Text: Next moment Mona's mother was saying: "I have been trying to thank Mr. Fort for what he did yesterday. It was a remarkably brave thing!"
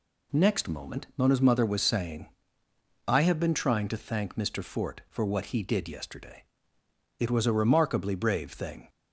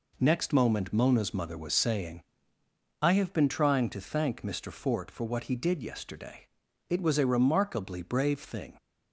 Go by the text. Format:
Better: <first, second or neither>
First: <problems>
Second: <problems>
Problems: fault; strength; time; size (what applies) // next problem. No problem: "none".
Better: neither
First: none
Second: none